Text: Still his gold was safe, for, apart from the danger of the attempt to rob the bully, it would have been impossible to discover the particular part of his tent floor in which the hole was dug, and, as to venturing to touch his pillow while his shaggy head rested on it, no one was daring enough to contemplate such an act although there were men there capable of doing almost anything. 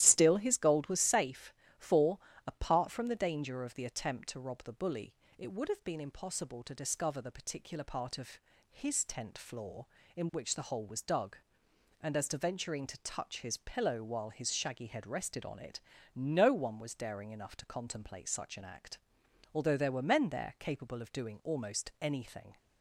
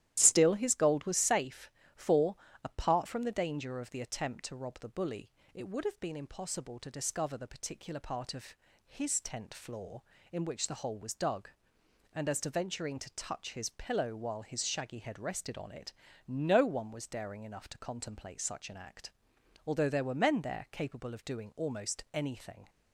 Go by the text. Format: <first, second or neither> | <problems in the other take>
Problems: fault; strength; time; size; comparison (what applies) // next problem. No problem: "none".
neither | starts louder than the rest; strong; the same in both // pauses between "of" and "his"; slight; the same in both // pauses between "act" and "although"; noticeable; the same in both